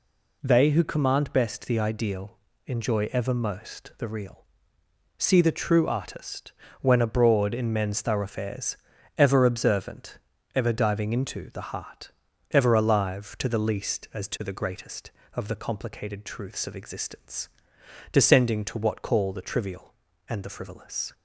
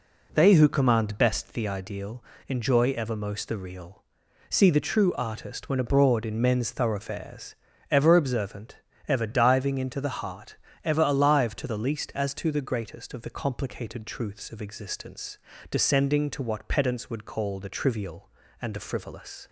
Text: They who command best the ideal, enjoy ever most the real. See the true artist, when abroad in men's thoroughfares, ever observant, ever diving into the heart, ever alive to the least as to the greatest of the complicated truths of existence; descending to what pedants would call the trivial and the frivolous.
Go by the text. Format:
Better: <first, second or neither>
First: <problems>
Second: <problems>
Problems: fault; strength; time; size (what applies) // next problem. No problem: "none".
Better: second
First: skips "pedants would"; at 19.0 s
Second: none